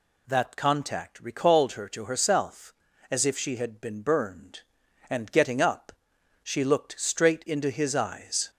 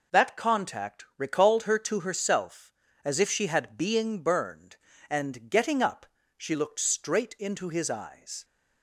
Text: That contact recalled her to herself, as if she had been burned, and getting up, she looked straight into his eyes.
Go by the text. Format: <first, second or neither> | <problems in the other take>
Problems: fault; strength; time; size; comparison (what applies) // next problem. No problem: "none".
first | says "being" for "been"; at 3.7 s